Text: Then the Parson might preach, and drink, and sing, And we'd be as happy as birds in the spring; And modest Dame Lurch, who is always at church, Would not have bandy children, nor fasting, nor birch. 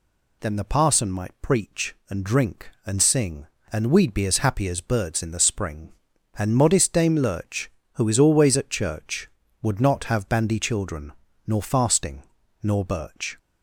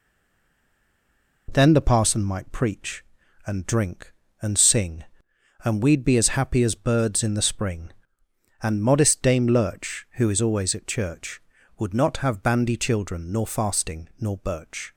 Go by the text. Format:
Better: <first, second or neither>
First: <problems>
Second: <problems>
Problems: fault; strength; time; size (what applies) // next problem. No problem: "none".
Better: first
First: none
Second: stays silent before the first word; noticeable; until 1.4 s; 1.4 s long